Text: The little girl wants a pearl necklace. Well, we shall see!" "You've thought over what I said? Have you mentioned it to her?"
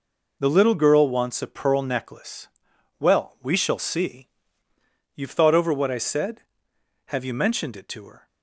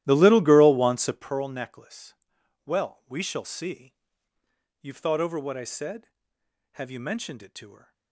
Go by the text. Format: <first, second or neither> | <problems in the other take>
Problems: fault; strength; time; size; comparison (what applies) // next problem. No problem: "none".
first | starts louder than the rest; strong; until 1.3 s; 14 dB